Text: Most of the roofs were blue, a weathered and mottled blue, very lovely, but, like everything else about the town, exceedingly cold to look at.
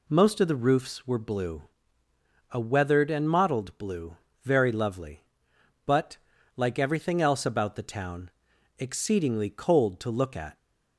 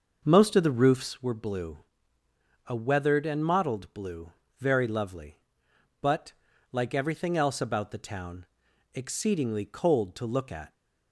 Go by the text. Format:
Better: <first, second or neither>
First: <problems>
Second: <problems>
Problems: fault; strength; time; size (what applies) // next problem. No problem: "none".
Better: first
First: none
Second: starts louder than the rest; noticeable; until 1.2 s; 6 dB